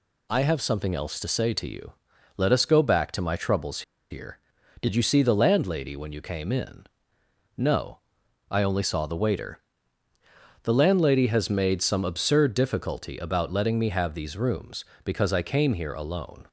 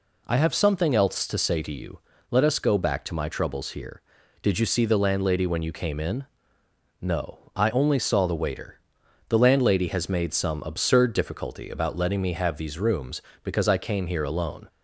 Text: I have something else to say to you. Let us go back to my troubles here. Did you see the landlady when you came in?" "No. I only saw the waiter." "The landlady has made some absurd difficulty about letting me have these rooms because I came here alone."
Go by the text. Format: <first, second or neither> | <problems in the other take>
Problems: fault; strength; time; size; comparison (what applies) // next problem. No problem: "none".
second | pauses between "troubles" and "here"; slight; at 3.8 s; 0.29 s long